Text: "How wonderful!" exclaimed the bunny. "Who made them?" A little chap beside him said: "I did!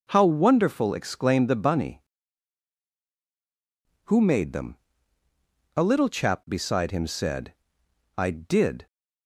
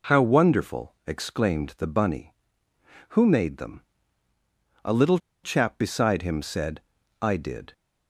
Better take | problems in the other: first | pauses between "little" and "chap"; slight; at 5.1 s; 0.26 s long

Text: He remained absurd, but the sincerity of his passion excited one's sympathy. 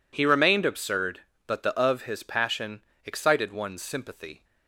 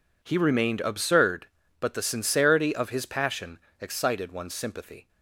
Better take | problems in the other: second | skips "sincerity"; at 1.7 s // pauses between "passion" and "excited"; slight; at 2.8 s; 0.20 s long; slight in the second

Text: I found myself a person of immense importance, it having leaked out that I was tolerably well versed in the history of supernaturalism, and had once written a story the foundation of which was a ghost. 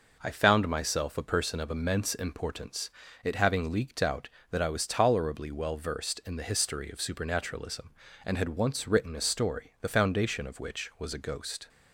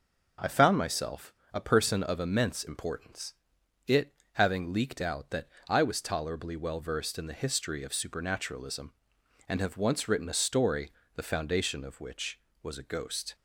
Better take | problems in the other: first | pauses between "myself" and "a"; slight; at 1.3 s; 0.19 s long // pauses between "it" and "having"; slight; at 4.1 s; 0.18 s long // pauses between "that" and "I"; slight; at 5.4 s; 0.22 s long // says "have" for "had"; at 9.6 s // pauses between "story" and "the"; slight; at 10.9 s; 0.24 s long

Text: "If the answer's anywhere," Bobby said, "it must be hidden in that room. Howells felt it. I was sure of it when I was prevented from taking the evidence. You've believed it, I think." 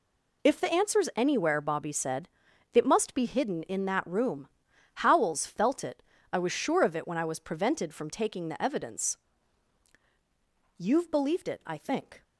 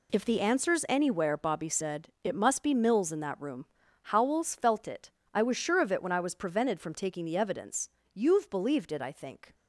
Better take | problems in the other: first | says "mills" for "hidden"; at 2.7 s

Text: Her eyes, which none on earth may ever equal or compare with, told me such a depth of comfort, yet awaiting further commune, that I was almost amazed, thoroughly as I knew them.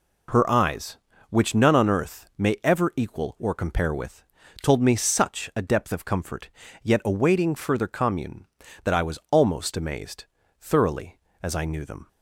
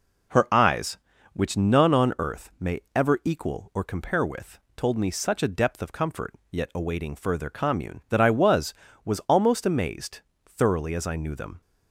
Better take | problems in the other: first | says "was" twice; at 9.0 s

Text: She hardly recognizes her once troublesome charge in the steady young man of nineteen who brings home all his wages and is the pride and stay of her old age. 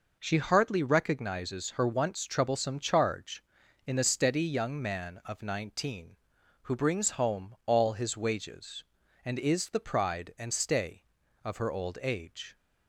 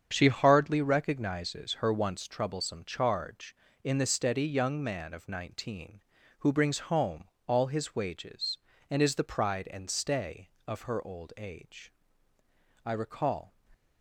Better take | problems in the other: first | starts louder than the rest; strong; until 1.1 s; 8 dB // pauses between "home" and "all"; slight; at 7.2 s; 0.16 s long // goes on to say "I recall"; noticeable; from 12.8 s on; 0.70 s long

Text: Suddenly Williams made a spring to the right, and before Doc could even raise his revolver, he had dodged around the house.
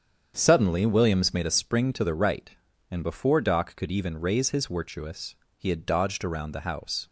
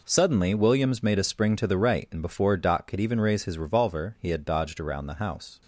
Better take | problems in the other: second | starts louder than the rest; strong; until 1.3 s; 7.5 dB // says "wirtuous" for "revolver"; at 4.6 s

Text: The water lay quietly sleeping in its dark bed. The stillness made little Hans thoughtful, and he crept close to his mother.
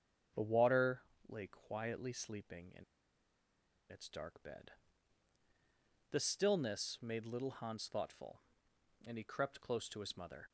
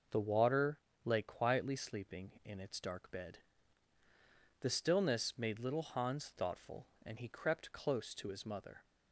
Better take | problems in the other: second | starts louder than the rest; strong; until 1.6 s; 7.5 dB // pauses between "water" and "lay"; slight; at 1.0 s; 0.28 s long; slight in the second // pauses between "in" and "its"; at 2.8 s; 1.0 s long

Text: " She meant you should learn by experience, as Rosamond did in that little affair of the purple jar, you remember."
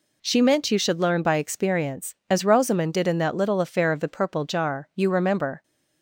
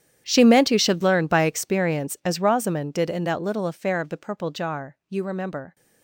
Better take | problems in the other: first | gets quieter; strong; throughout; 20 dB

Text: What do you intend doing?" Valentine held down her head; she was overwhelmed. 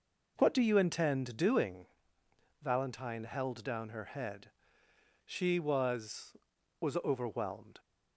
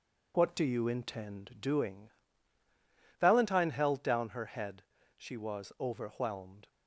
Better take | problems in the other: second | says "was" twice; at 6.8 s

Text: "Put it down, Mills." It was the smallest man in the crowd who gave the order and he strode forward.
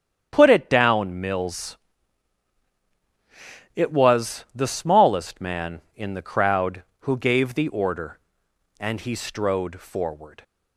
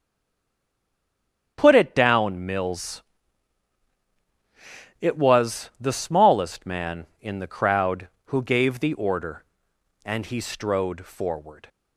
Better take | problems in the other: first | stays silent before the first word; noticeable; until 1.5 s; 1.5 s long // starts louder than the rest; strong; until 2.5 s; 9 dB; strong in the first

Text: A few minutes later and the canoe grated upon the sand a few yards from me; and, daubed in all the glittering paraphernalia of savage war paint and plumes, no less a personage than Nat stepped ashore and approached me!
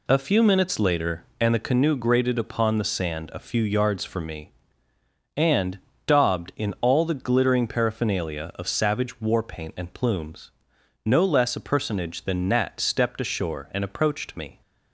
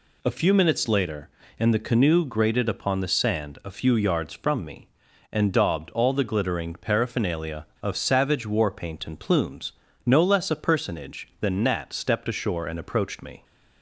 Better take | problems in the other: first | skips "in"; at 5.9 s

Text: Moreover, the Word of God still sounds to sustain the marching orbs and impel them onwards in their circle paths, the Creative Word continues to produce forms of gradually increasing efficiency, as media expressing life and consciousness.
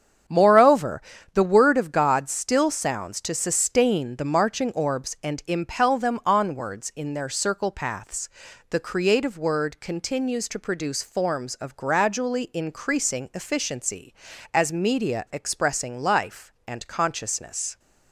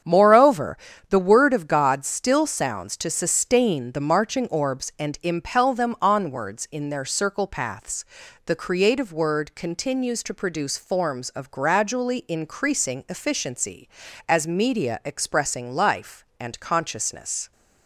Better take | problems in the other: neither | starts louder than the rest; strong; the same in both

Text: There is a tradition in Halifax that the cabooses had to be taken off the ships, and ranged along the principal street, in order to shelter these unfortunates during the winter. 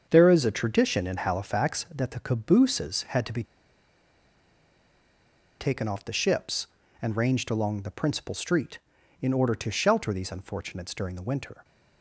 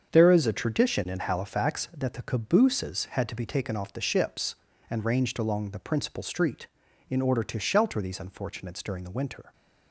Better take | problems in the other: second | starts louder than the rest; strong; until 1.1 s; 7 dB; strong in the second // pauses between "be" and "taken"; strong; at 3.4 s; 2.1 s long

